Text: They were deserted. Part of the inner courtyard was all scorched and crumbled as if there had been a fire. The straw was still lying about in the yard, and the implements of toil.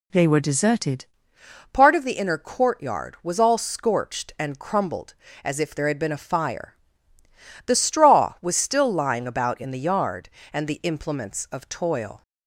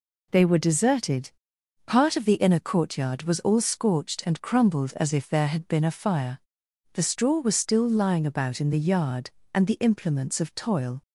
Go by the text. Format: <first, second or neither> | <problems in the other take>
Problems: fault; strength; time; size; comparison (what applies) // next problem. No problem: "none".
second | changes voice at "Part"; from 1.7 s on; 10.5 s long